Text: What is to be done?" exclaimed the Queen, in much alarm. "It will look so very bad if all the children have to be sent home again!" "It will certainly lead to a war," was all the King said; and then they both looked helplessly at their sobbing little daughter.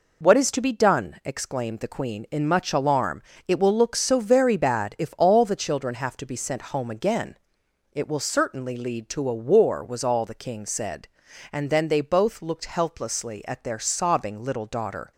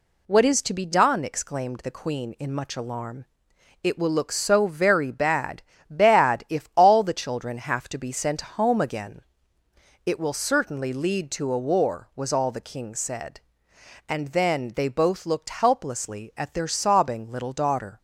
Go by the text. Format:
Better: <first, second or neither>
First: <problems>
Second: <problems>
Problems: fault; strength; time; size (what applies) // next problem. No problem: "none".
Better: first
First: none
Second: says "bad" twice; at 5.8 s